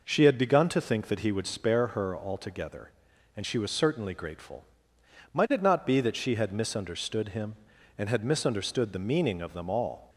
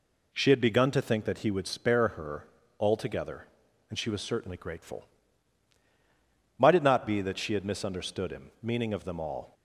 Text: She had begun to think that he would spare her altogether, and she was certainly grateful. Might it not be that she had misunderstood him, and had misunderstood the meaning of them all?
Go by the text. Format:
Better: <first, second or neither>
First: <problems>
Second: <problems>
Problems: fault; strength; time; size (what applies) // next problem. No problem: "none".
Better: first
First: none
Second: pauses between "her" and "altogether"; slight; at 2.4 s; 0.32 s long // skips "and had misunderstood the"; at 8.5 s